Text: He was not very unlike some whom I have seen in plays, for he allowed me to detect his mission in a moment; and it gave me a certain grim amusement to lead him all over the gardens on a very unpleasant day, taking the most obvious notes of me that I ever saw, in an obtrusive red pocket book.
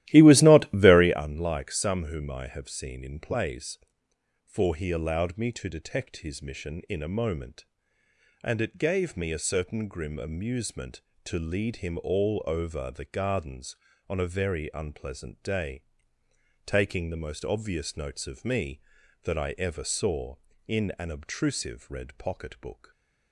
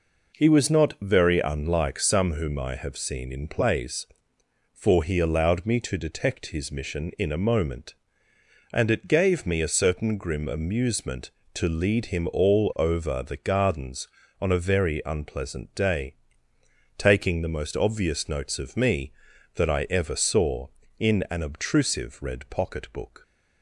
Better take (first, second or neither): second